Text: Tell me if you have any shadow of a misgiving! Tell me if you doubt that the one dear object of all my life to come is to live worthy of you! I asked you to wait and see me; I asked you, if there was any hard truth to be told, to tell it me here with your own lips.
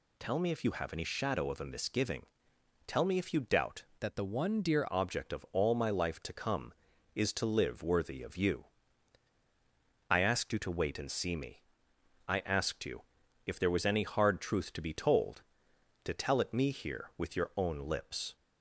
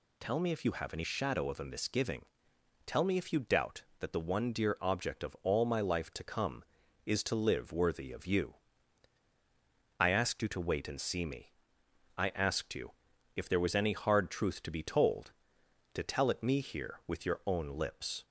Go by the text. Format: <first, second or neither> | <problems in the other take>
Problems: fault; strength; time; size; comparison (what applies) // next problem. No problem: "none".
second | changes voice from "that" to "dear"; from 3.9 to 4.8 s; 0.9 s long